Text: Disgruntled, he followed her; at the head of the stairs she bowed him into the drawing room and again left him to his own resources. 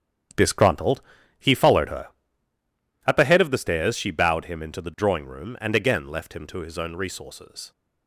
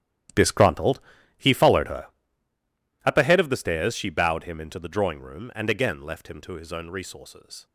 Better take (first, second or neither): first